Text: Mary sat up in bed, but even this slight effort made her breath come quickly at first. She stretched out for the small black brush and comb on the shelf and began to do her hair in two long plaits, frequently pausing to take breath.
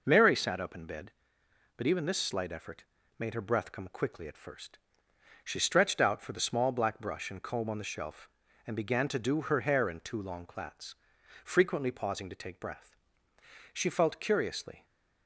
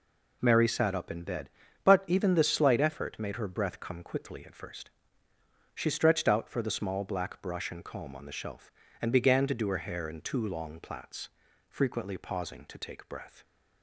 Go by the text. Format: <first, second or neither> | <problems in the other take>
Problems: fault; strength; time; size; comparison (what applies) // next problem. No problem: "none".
second | pauses between "effort" and "made"; slight; at 2.8 s; 0.34 s long // goes on to say "She felt curiously"; noticeable; from 13.7 s on; 1.1 s long